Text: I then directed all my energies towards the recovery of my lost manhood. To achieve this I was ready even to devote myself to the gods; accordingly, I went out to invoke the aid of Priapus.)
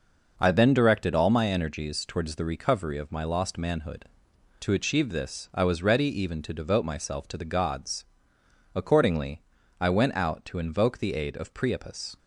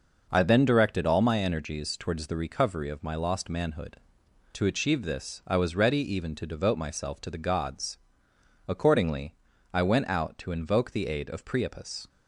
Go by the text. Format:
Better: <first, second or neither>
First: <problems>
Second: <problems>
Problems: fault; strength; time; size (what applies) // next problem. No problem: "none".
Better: neither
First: none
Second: none